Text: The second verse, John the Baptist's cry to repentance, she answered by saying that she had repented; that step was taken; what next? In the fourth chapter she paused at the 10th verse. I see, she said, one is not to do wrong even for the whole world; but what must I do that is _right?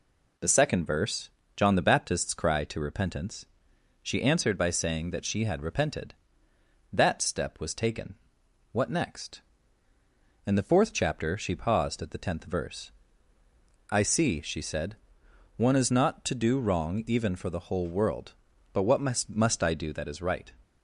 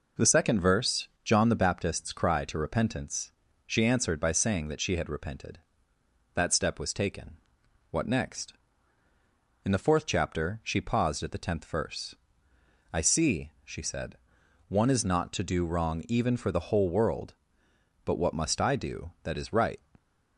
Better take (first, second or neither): second